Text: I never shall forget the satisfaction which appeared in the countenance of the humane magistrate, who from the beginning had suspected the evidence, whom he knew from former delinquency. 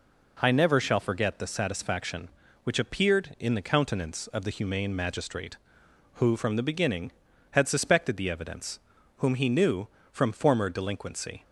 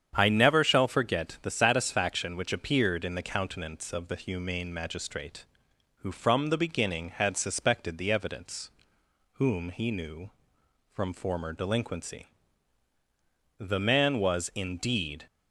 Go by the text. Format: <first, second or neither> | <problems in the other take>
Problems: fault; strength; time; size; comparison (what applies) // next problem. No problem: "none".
first | starts louder than the rest; strong; until 1.1 s; 8.5 dB // goes on to say "The man was indeed"; from 13.6 s on; 1.6 s long